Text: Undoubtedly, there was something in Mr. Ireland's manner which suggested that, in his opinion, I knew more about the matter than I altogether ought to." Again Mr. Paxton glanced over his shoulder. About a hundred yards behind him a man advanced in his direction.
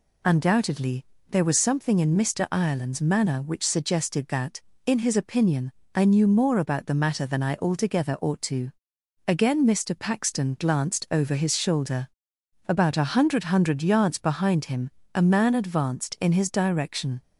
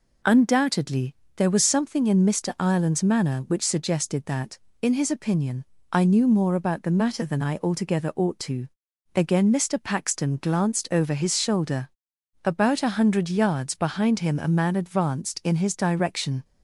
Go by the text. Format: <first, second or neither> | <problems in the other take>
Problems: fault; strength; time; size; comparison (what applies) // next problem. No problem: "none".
second | says "hundred" twice; at 13.4 s // pauses between "him" and "a"; slight; at 14.8 s; 0.26 s long